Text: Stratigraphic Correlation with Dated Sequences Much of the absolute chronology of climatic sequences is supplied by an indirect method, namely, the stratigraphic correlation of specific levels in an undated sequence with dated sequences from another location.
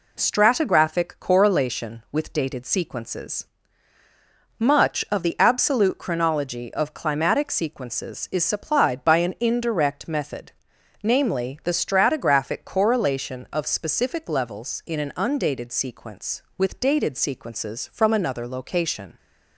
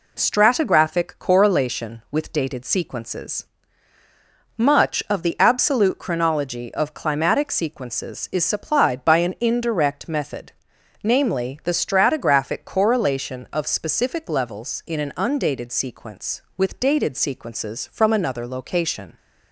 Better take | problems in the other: neither | pauses between "Sequences" and "Much"; the same in both

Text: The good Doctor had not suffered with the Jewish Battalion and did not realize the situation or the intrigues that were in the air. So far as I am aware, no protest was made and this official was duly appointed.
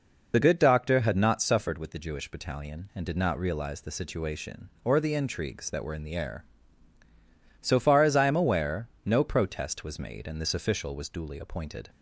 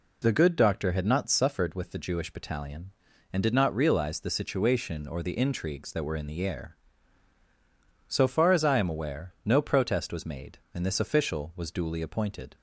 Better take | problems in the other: second | loses the start of "The"; at 0.3 s; 45 ms

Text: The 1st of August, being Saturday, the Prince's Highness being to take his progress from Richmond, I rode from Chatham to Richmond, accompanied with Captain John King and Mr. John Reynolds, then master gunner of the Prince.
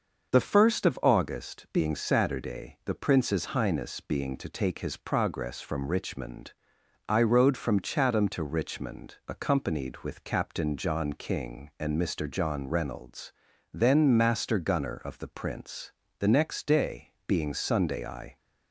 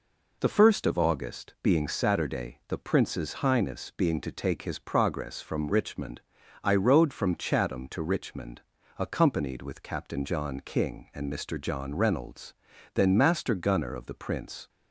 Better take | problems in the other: second | starts louder than the rest; until 1.3 s; 6.5 dB // goes on to say "The next day being Sunday I"; strong; from 16.1 s on; 2.1 s long

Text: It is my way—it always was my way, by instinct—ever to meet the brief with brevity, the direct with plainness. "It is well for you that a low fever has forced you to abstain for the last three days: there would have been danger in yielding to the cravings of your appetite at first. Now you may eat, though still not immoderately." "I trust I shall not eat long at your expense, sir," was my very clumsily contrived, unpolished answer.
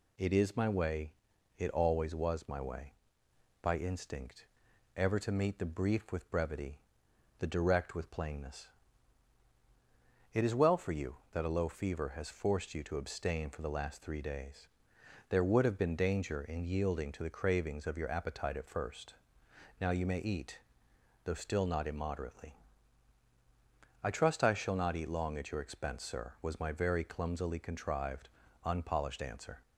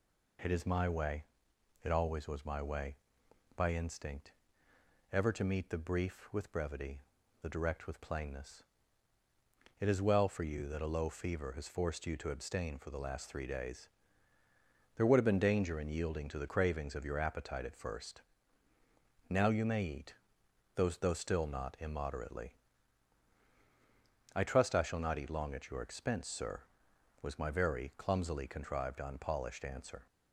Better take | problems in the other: first | says "though" twice; at 20.8 s

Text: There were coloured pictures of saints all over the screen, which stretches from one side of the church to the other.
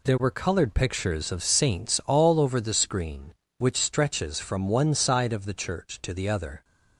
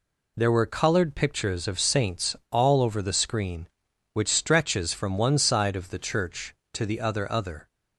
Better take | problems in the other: first | pauses between "saints" and "all"; slight; at 2.3 s; 0.17 s long // says "other" twice; at 7.3 s

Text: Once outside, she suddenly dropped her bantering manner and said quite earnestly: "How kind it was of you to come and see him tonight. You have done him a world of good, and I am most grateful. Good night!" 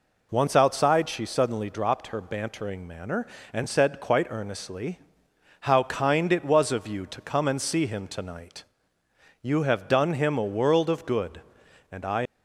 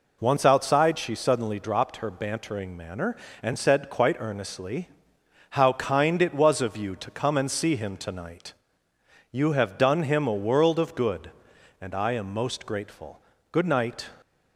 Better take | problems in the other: second | stops before "am most grateful Good night"; at 12.2 s

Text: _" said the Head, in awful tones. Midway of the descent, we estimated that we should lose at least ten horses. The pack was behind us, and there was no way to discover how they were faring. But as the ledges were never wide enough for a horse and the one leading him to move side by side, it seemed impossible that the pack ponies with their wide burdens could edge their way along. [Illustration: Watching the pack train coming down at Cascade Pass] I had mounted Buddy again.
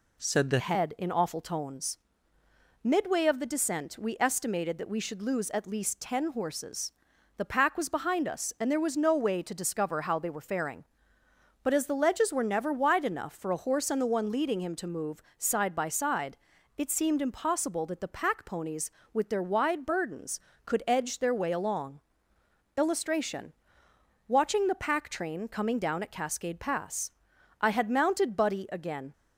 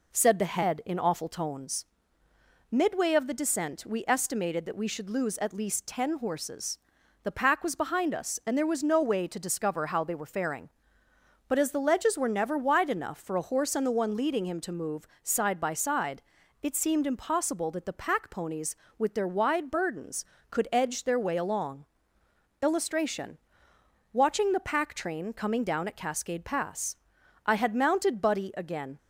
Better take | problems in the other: second | changes voice from "said" to "the"; from 0.2 to 0.5 s; 0.3 s long // pauses between "move" and "side"; slight; at 15.2 s; 0.16 s long; slight in the second // pauses between "Pass" and "I"; noticeable; at 27.1 s; 0.50 s long; noticeable in the second

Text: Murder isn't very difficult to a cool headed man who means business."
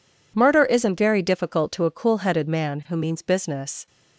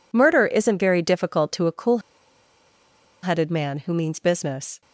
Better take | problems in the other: first | pauses between "cool" and "headed"; at 1.9 s; 1.2 s long

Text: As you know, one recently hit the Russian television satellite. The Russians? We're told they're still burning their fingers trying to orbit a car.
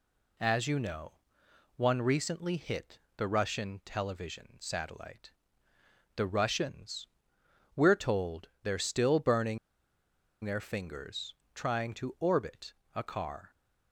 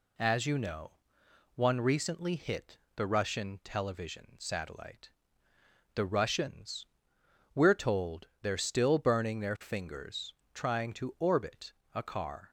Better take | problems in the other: second | pauses between "hit" and "the"; slight; at 2.9 s; 0.18 s long; slight in the second // pauses between "burning" and "their"; noticeable; at 9.5 s; 0.86 s long // pauses between "fingers" and "trying"; slight; at 11.3 s; 0.20 s long; slight in the second // pauses between "orbit" and "a"; slight; at 12.7 s; 0.22 s long; slight in the second

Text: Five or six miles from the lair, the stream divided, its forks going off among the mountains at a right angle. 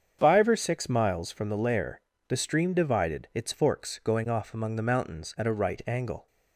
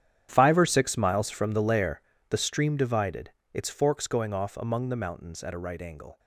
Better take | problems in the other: first | gets quieter; strong; throughout; 16.5 dB // starts louder than the rest; strong; until 1.3 s; 10.5 dB; strong in the first

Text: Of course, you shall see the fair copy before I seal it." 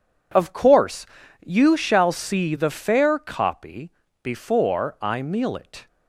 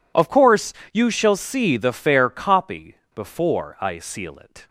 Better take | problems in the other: second | pauses between "copy" and "before"; slight; at 3.9 s; 0.32 s long; slight in the second // says "meal" for "seal"; at 5.2 s

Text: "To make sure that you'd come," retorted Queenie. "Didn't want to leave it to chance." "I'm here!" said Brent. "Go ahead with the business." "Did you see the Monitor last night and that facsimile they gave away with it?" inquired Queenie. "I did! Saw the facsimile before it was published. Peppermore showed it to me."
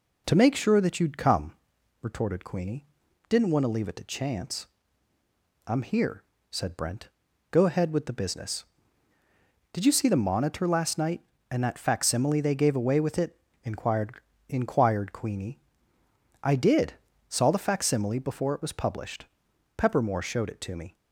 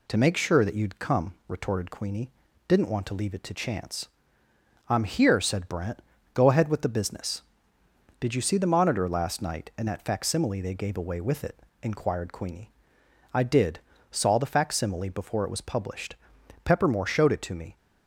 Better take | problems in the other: second | says "inquired" twice; at 14.4 s

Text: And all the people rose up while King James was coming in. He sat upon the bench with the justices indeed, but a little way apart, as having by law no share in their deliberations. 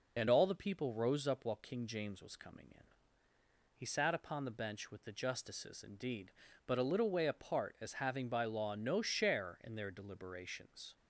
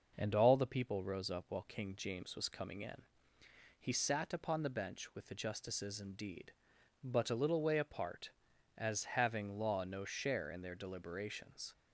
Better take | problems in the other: first | skips "by"; at 9.5 s

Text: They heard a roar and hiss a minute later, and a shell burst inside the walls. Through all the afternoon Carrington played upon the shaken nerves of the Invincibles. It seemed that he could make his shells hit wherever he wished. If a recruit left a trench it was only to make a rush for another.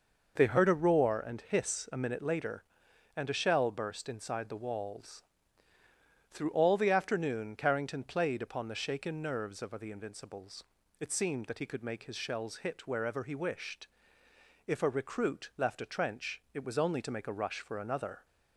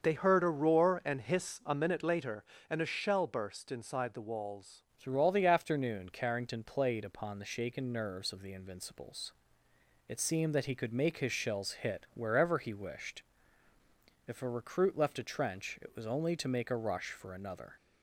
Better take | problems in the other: first | starts louder than the rest; until 1.0 s; 6.5 dB // changes voice at "Through"; from 4.9 s on; 12.8 s long

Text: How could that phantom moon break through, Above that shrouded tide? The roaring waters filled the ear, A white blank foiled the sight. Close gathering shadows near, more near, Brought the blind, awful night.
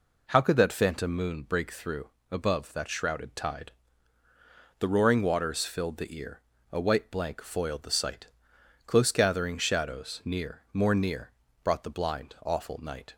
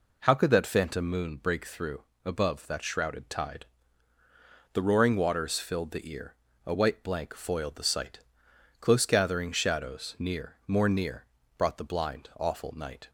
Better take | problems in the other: neither | none

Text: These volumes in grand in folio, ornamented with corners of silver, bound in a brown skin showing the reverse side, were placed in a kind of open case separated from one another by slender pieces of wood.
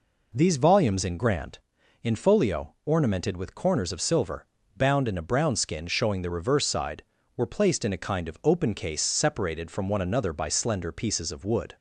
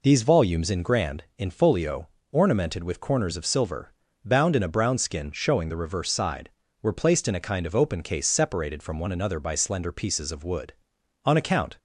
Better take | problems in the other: first | goes on to say "On account"; from 11.2 s on; 0.50 s long

